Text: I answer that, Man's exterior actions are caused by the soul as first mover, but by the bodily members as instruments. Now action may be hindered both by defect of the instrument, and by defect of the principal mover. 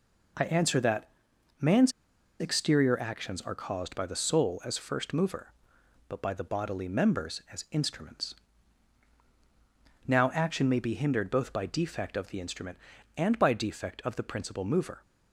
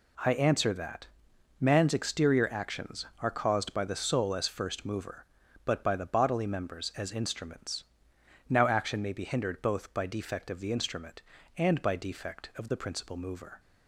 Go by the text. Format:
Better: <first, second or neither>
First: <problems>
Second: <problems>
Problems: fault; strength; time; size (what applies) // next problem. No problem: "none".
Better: second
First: pauses between "Man's" and "exterior"; noticeable; at 1.9 s; 0.50 s long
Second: none